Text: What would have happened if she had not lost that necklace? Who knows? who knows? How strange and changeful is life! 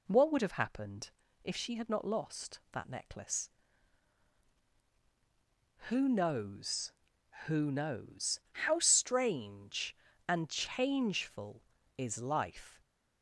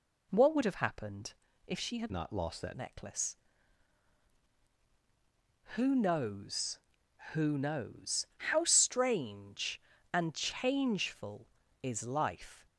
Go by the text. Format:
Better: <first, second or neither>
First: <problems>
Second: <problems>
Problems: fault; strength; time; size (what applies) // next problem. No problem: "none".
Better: first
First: pauses between "happened" and "if"; slight; at 1.0 s; 0.34 s long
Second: pauses between "happened" and "if"; slight; at 1.3 s; 0.34 s long // changes voice from "not" to "that"; from 2.1 to 2.7 s; 0.6 s long